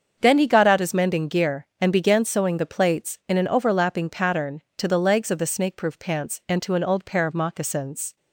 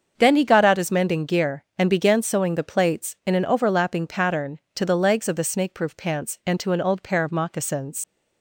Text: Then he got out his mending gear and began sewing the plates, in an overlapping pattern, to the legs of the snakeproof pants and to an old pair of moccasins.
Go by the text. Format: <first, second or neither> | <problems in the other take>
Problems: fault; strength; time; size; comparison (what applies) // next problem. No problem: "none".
first | starts louder than the rest; until 1.1 s; 7 dB; also in the first // leaves "moccasins" unfinished; at 8.0 s; 90 ms